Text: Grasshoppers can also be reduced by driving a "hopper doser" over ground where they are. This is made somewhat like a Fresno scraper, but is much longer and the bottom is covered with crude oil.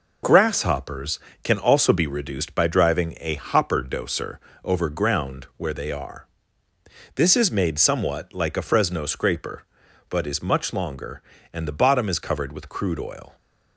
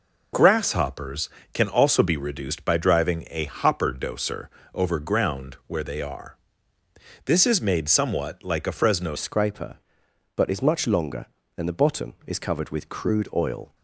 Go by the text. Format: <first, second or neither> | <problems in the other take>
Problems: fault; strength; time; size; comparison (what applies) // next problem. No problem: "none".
first | pauses between "doser" and "over"; slight; at 4.4 s; 0.26 s long; slight in the first // changes voice at "scraper"; from 9.1 s on; 4.6 s long